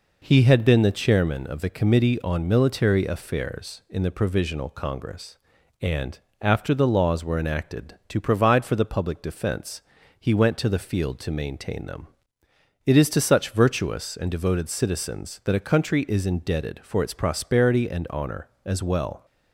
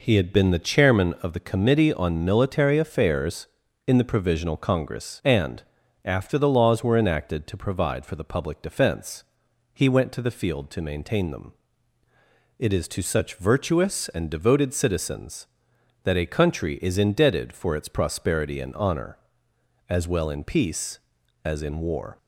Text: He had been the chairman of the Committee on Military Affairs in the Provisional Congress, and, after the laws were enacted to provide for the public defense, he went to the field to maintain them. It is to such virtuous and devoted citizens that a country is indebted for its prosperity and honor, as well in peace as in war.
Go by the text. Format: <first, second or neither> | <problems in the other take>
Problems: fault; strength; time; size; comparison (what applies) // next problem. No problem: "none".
second | stops before "in peace as in war"; at 19.2 s